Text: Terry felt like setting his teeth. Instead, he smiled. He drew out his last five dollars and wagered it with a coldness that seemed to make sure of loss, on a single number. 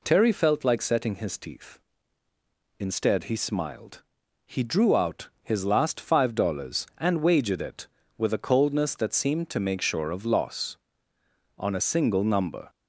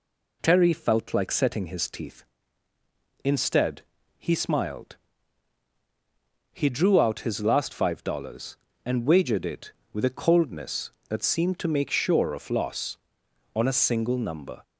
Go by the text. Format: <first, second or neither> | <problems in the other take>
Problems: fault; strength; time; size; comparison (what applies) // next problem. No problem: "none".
neither | none